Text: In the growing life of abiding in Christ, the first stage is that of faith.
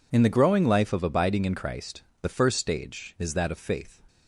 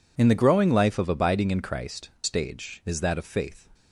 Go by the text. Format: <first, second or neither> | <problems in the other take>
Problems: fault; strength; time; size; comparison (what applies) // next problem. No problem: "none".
first | skips "the first"; at 2.1 s